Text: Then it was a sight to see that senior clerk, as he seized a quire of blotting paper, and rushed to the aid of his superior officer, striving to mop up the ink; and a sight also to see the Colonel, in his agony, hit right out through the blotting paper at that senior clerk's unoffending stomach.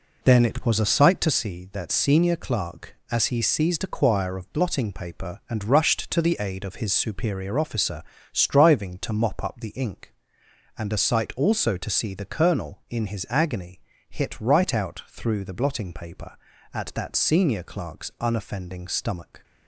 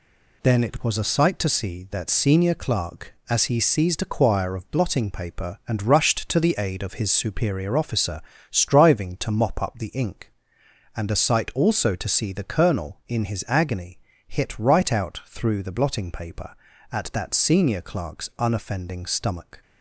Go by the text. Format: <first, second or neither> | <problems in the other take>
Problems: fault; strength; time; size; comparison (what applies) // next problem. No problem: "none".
second | starts louder than the rest; until 1.5 s; 3.5 dB